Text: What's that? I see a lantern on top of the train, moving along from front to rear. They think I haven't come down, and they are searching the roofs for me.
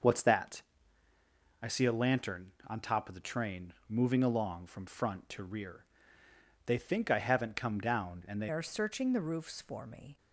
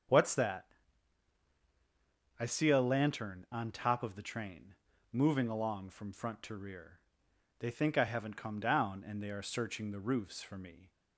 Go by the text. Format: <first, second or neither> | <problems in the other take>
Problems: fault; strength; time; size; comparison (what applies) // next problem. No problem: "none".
second | starts louder than the rest; noticeable; until 2.0 s; 6 dB; strong in the second // changes voice at "are"; from 8.5 s on; 1.6 s long